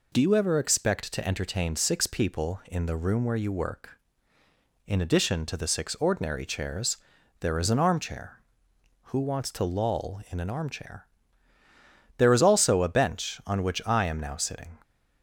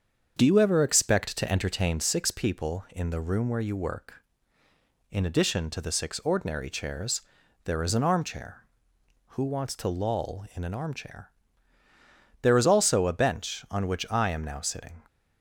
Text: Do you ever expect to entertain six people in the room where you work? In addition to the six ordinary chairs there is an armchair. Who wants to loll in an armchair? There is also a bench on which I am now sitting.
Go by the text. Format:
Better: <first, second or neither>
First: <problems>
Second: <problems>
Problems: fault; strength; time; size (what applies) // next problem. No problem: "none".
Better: first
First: pauses between "chairs" and "there"; at 6.9 s; 0.42 s long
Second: starts louder than the rest; strong; until 2.2 s; 7 dB // pauses between "chairs" and "there"; at 7.2 s; 0.42 s long